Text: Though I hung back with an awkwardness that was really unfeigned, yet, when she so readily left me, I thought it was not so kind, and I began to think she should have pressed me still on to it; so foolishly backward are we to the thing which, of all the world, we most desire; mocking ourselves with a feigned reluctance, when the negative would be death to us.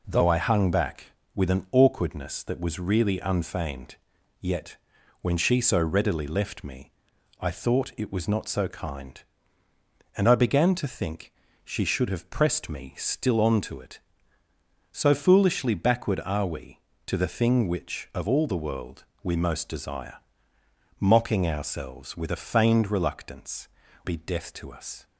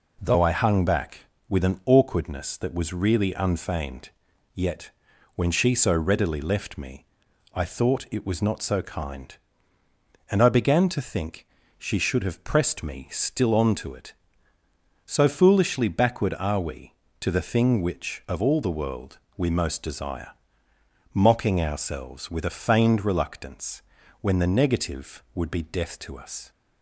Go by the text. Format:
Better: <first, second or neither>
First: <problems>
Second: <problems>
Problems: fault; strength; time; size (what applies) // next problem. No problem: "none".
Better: second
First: pauses between "think" and "she"; slight; at 11.3 s; 0.32 s long // skips "when the negative would"; at 23.8 s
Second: pauses between "think" and "she"; slight; at 11.4 s; 0.32 s long